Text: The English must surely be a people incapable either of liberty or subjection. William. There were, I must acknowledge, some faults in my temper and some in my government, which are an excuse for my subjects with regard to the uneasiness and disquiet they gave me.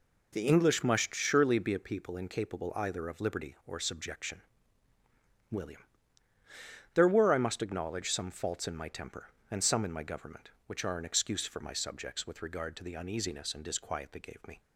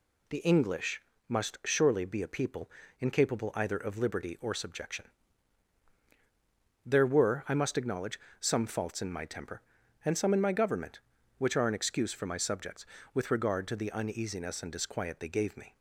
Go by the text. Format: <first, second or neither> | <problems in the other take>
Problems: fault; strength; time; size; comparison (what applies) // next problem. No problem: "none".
first | pauses between "English" and "must"; slight; at 1.0 s; 0.28 s long // pauses between "people" and "incapable"; slight; at 2.6 s; 0.30 s long // skips "William"; at 5.9 s